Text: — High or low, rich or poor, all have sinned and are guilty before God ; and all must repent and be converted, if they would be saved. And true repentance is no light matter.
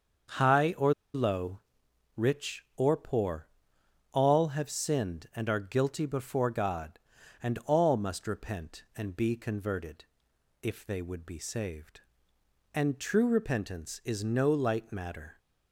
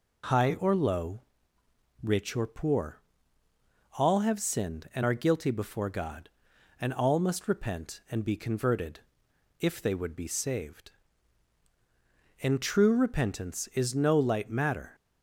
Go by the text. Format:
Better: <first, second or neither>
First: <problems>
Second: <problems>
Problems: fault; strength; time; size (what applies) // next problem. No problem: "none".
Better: second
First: starts louder than the rest; until 1.5 s; 6.5 dB // pauses between "or" and "low"; slight; at 0.9 s; 0.20 s long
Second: none